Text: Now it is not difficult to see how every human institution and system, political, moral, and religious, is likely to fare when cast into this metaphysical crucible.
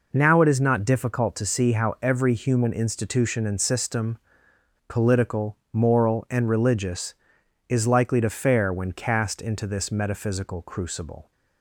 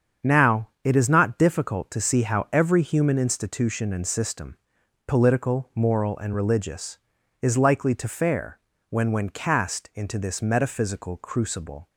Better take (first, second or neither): first